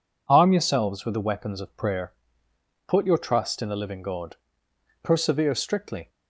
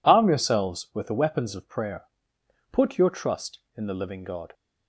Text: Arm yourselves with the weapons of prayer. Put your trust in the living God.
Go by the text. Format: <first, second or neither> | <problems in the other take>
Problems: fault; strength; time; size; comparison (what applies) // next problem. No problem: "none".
second | goes on to say "Persevere strictly"; noticeable; from 5.0 s on; 1.0 s long